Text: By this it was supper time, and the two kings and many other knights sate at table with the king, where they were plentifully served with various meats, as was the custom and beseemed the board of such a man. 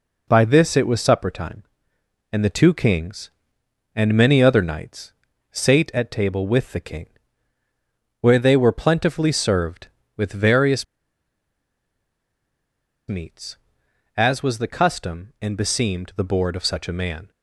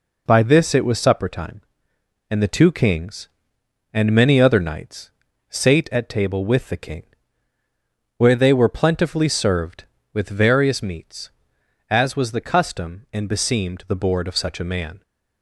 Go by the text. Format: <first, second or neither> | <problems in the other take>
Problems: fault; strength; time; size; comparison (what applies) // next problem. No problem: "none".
second | pauses between "knights" and "sate"; at 5.1 s; 0.38 s long; also in the second // pauses between "various" and "meats"; strong; at 10.8 s; 2.2 s long